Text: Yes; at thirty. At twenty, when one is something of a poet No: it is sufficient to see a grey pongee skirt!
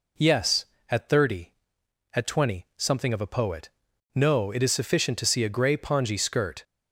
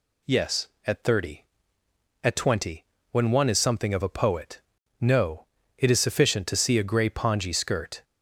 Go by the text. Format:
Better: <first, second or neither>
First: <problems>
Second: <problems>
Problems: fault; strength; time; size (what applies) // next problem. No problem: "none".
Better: second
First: skips "when one is"; at 2.7 s // pauses between "poet" and "No"; noticeable; at 3.6 s; 0.48 s long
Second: pauses between "poet" and "No"; at 4.6 s; 0.38 s long